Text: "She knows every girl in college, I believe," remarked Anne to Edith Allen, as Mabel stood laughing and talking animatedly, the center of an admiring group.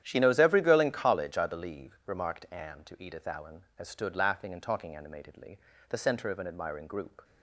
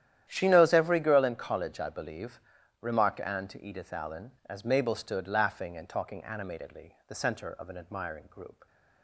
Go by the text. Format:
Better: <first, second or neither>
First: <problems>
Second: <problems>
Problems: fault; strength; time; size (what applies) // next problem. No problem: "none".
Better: second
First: starts louder than the rest; strong; until 1.0 s; 10.5 dB // skips "Mabel"; at 3.8 s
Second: starts louder than the rest; strong; until 1.3 s; 11 dB